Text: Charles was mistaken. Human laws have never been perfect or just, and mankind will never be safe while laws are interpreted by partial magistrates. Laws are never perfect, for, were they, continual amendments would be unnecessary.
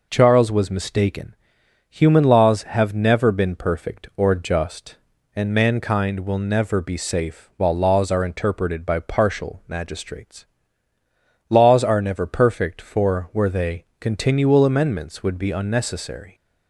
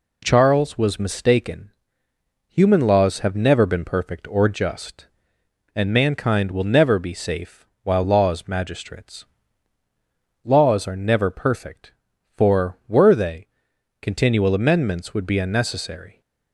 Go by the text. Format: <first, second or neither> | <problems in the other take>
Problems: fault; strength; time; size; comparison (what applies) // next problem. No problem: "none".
first | pauses between "safe" and "while"; slight; at 7.6 s; 0.16 s long // skips "are interpreted by partial"; at 8.4 s